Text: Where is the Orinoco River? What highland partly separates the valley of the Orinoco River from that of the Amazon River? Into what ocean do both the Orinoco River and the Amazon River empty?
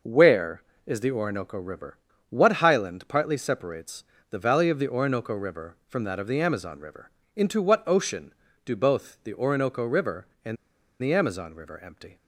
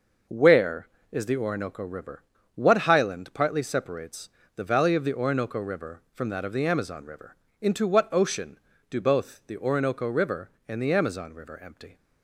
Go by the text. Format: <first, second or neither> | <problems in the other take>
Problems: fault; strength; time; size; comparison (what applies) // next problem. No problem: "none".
second | pauses between "separates" and "the"; slight; at 4.0 s; 0.28 s long; slight in the second // pauses between "and" and "the"; noticeable; at 10.5 s; 0.46 s long